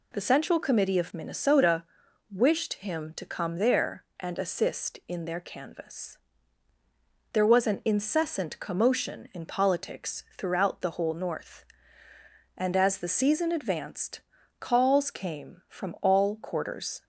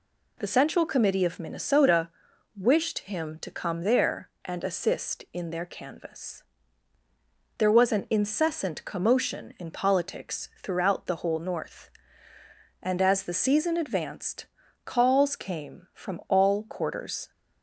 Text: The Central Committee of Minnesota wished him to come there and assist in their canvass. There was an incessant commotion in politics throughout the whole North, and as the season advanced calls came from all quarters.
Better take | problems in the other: neither | pauses between "Minnesota" and "wished"; noticeable; the same in both // pauses between "politics" and "throughout"; slight; the same in both // pauses between "advanced" and "calls"; the same in both

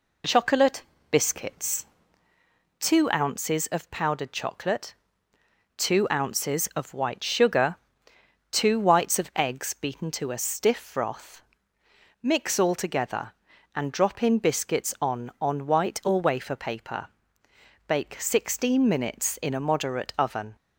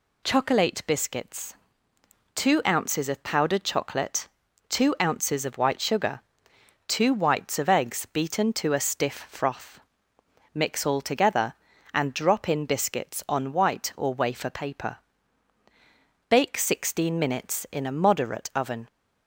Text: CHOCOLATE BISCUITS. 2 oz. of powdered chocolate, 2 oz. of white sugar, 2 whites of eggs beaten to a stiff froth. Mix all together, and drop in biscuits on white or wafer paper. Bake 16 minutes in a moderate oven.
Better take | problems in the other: second | pauses between "CHOCOLATE" and "BISCUITS"; slight; at 0.8 s; 0.30 s long // says "on" twice; at 15.3 s

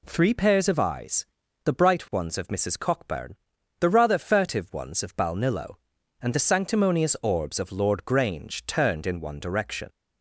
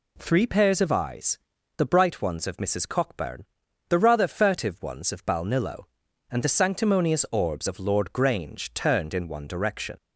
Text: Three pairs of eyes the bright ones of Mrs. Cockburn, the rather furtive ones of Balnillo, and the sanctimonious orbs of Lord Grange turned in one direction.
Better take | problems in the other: neither | pauses between "eyes" and "the"; the same in both

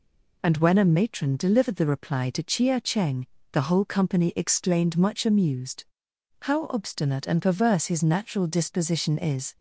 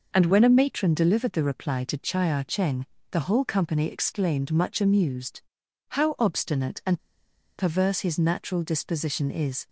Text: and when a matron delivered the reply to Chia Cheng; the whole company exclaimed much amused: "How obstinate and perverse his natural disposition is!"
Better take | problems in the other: first | pauses between "and" and "perverse"; noticeable; at 6.9 s; 0.61 s long

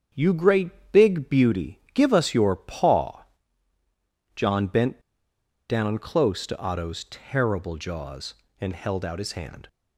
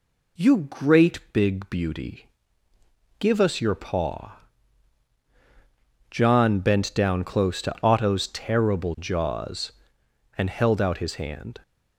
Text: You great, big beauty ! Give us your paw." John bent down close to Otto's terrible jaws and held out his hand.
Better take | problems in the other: second | starts louder than the rest; strong; until 1.3 s; 7.5 dB // pauses between "bent" and "down"; noticeable; at 5.0 s; 0.69 s long

